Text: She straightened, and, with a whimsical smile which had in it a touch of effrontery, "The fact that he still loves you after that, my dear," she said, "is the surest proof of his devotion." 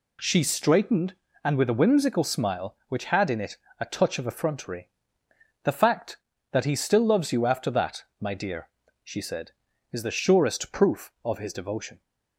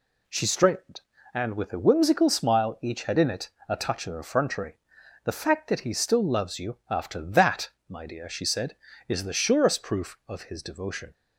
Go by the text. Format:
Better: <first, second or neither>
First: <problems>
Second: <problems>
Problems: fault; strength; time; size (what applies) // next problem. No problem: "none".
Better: first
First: pauses between "it" and "a"; slight; at 3.5 s; 0.24 s long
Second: says "each" for "which"; at 2.8 s // pauses between "it" and "a"; slight; at 3.5 s; 0.18 s long